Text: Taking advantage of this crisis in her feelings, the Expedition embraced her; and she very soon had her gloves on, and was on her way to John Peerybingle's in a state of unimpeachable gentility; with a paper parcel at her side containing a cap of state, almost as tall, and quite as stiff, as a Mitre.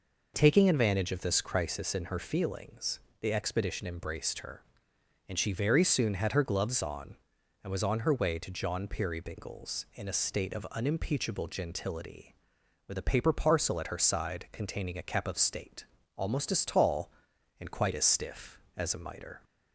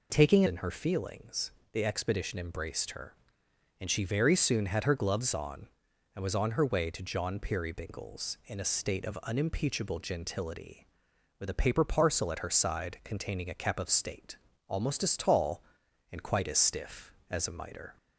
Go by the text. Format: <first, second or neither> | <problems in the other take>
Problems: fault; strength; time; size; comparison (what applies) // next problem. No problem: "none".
first | skips "advantage of this crisis"; at 0.4 s